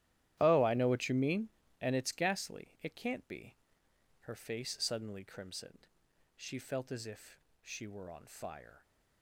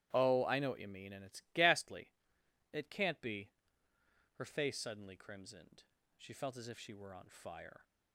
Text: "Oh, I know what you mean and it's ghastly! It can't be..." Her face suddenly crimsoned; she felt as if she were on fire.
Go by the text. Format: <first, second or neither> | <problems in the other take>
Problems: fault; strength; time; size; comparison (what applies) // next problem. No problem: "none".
second | gets quieter; strong; throughout; 15.5 dB // starts louder than the rest; strong; until 1.4 s; 12.5 dB; strong in the second // pauses between "if" and "she"; slight; at 7.3 s; 0.24 s long